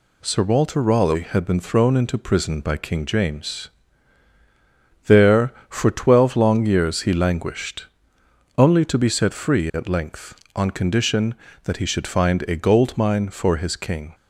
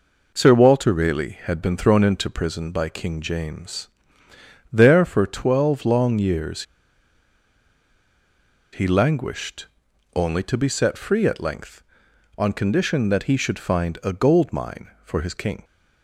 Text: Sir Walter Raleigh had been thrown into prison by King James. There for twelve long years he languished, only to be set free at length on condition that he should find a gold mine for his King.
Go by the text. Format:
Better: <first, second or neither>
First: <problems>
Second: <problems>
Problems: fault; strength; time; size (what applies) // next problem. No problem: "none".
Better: first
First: none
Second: pauses between "years" and "he"; strong; at 6.6 s; 2.1 s long